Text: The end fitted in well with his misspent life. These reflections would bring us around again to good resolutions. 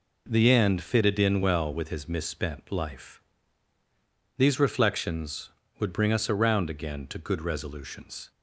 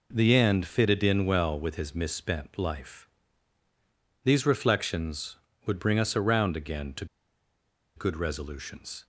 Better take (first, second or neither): first